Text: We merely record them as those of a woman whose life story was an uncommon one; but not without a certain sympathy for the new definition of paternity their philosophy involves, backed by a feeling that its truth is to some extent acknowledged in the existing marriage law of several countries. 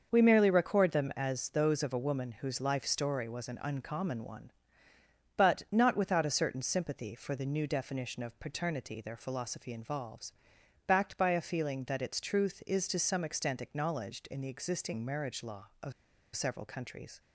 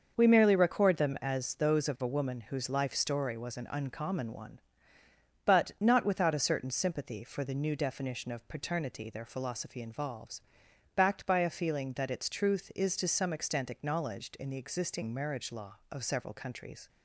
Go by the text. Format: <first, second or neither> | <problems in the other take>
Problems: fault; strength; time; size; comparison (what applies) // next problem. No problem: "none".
second | starts louder than the rest; until 1.1 s; 6.5 dB; also in the second // pauses between "of" and "several"; at 15.9 s; 0.43 s long